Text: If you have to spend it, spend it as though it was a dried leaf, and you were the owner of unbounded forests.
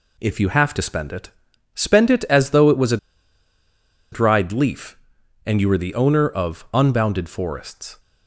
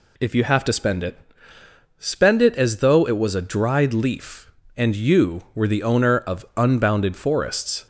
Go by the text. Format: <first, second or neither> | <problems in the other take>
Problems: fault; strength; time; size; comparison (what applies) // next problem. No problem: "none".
second | pauses between "a" and "dried"; at 2.9 s; 1.1 s long